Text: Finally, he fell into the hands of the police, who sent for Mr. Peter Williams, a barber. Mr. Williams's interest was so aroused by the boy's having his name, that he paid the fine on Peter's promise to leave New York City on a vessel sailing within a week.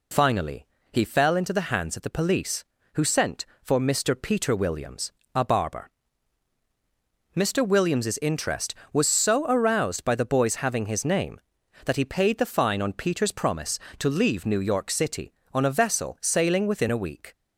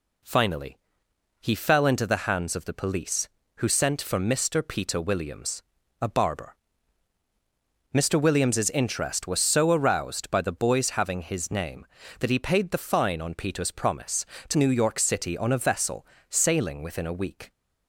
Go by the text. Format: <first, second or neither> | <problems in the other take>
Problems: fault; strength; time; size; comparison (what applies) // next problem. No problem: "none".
first | skips "leave"; at 14.5 s // pauses between "vessel" and "sailing"; slight; at 16.0 s; 0.24 s long